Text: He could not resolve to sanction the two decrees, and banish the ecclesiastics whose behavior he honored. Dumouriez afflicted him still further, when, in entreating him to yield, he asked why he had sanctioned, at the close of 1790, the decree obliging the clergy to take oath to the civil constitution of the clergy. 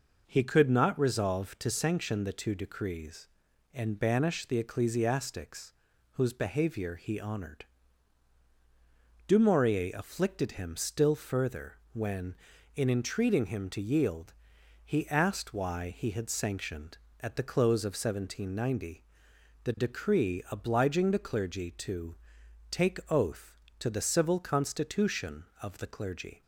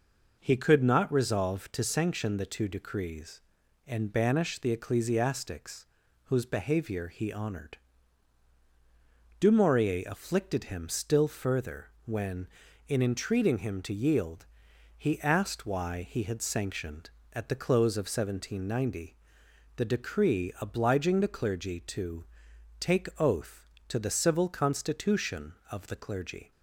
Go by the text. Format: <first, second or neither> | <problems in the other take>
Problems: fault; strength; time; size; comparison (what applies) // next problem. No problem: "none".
neither | pauses between "ecclesiastics" and "whose"; the same in both // pauses between "to" and "take"; noticeable; the same in both